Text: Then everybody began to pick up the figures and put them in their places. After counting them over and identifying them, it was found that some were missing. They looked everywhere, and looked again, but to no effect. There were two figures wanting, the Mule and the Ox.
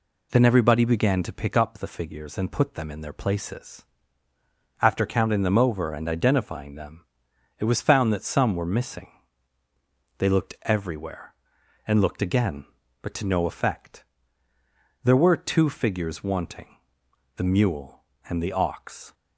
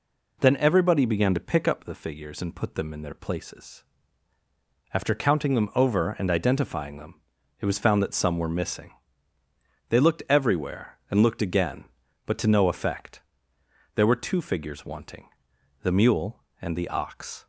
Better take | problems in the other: neither | none

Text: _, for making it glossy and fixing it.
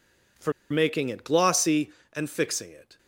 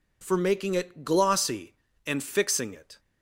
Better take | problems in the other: second | pauses between "for" and "making"; slight; at 0.5 s; 0.18 s long

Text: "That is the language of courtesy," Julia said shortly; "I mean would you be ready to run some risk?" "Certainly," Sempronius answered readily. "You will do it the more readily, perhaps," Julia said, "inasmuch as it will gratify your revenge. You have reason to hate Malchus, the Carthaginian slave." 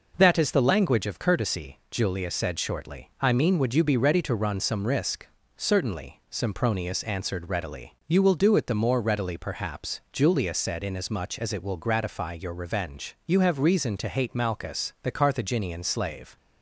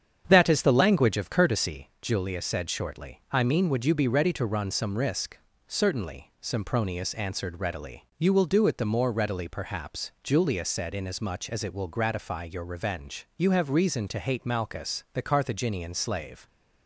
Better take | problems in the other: first | starts louder than the rest; strong; until 1.9 s; 8 dB

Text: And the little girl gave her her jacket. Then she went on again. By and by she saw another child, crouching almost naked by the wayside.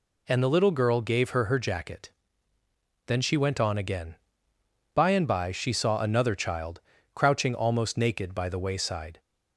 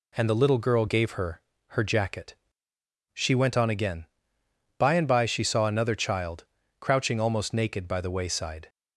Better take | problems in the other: first | pauses between "her" and "her"; slight; at 1.4 s; 0.28 s long // skips "Then"; at 2.7 s

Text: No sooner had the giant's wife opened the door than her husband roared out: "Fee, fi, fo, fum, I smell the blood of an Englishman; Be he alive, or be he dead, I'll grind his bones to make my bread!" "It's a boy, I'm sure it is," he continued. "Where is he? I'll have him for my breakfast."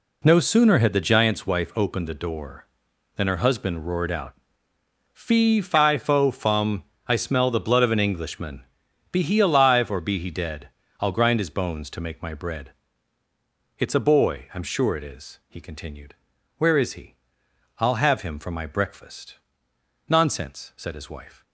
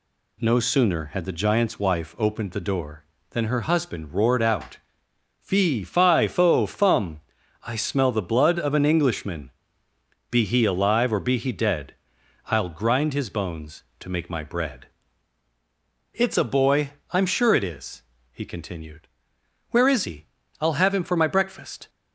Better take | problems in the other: second | goes on to say "Nonsense said his wife"; from 20.0 s on; 1.3 s long

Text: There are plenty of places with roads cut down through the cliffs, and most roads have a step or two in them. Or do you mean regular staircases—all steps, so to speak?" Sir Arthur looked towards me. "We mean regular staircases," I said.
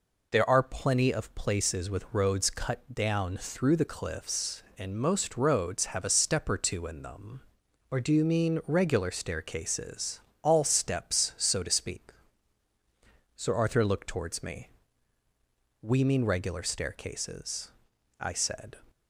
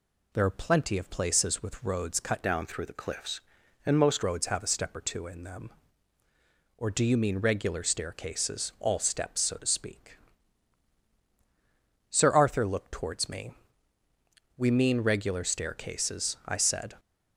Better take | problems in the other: first | changes voice from "down" to "most"; from 2.4 to 4.2 s; 1.8 s long

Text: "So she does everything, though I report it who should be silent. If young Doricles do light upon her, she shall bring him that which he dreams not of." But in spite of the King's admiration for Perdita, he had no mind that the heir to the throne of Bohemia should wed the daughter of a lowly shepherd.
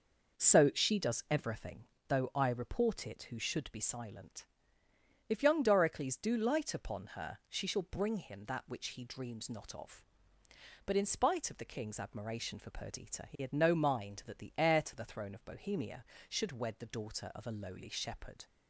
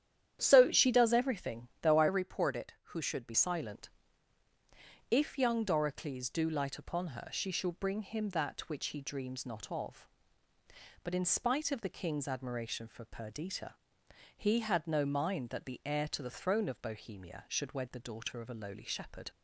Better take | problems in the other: first | starts louder than the rest; strong; until 1.4 s; 10 dB // changes voice from "report" to "be"; from 2.0 to 3.3 s; 1.3 s long

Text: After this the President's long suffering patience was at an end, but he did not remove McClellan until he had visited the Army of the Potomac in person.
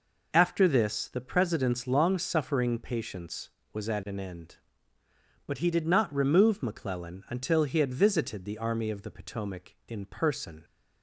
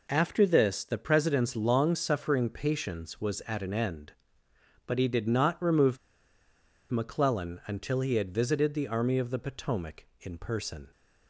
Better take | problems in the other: first | pauses between "remove" and "McClellan"; noticeable; at 5.9 s; 0.92 s long

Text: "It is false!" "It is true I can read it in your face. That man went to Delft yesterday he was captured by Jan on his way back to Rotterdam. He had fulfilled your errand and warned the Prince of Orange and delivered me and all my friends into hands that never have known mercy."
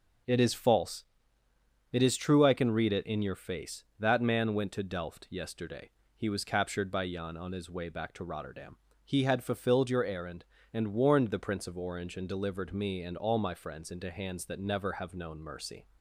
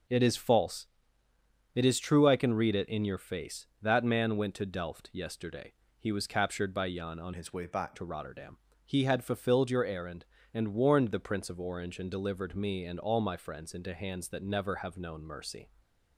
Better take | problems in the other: first | pauses between "yesterday" and "he"; slight; at 5.7 s; 0.26 s long; slight in the first // changes voice from "his" to "back"; from 7.3 to 7.9 s; 0.6 s long

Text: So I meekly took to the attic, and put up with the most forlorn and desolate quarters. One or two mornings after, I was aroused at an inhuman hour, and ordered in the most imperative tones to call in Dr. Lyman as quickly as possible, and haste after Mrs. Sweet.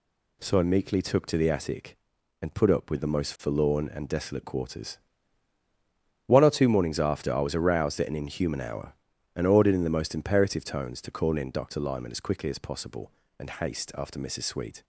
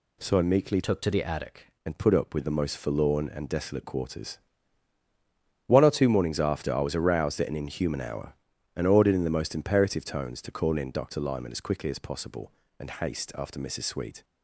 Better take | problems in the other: first | changes voice from "took" to "attic"; from 0.8 to 1.6 s; 0.8 s long

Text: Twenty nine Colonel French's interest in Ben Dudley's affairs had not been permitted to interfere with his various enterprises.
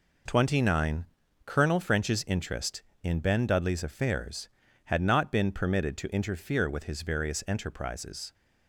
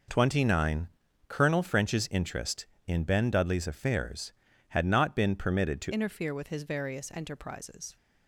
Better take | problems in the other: first | pauses between "nine" and "Colonel"; at 0.8 s; 0.40 s long; also in the first // changes voice at "interfere"; from 5.9 s on; 2.0 s long

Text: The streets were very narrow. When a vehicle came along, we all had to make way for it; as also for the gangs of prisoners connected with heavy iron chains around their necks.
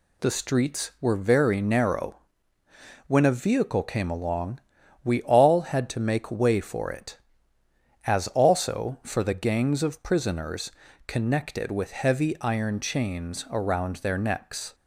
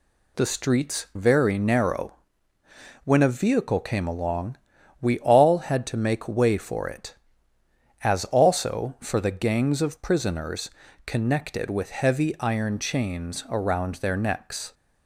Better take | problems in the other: first | skips "were"; at 1.1 s // pauses between "prisoners" and "connected"; slight; at 10.7 s; 0.34 s long; slight in the first

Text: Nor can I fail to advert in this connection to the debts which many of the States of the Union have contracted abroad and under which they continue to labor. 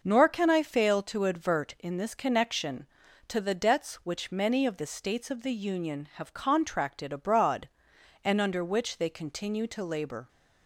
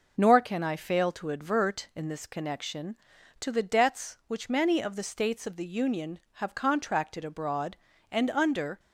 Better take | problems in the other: first | stops before "which they continue to labor"; at 8.7 s

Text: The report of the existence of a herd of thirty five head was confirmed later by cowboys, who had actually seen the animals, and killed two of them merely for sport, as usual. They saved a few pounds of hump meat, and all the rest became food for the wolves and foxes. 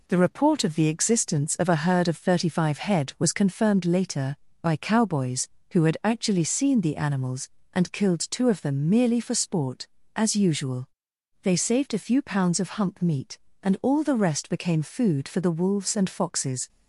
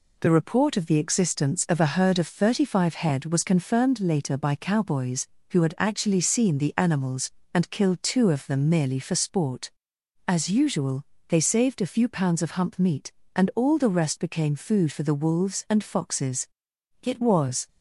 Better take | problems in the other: first | goes on to say "It was"; noticeable; from 17.0 s on; 0.64 s long

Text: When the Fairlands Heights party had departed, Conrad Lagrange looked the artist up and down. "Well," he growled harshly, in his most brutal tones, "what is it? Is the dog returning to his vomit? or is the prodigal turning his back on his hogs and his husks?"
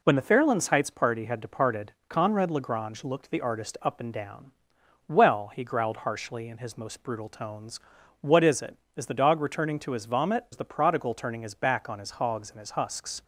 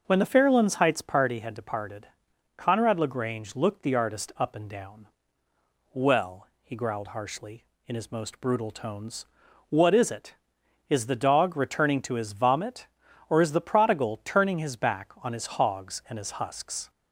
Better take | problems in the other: second | skips "or"; at 10.4 s

